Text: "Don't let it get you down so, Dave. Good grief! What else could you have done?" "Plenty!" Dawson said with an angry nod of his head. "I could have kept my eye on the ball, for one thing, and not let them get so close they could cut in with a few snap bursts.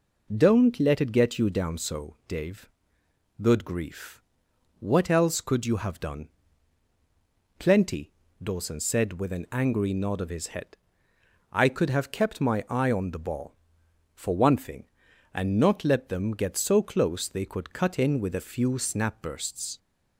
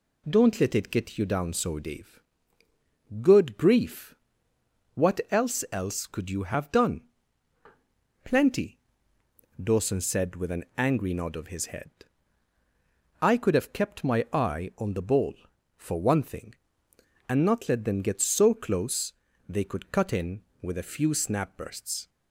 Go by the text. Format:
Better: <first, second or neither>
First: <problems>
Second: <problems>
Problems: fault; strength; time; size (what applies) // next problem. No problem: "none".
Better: first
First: none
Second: says "else" twice; at 5.7 s // pauses between "close" and "they"; slight; at 19.1 s; 0.36 s long